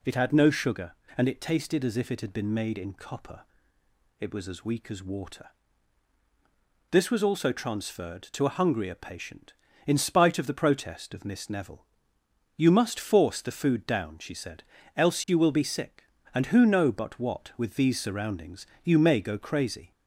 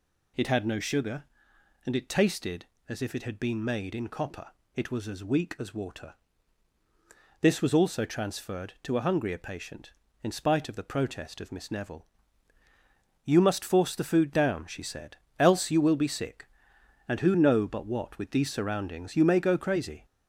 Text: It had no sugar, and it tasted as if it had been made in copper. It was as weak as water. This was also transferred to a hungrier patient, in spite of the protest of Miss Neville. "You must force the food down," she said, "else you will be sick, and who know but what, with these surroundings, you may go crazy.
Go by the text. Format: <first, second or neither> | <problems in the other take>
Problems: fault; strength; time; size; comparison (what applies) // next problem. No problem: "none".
first | gets louder; slight; throughout; 3 dB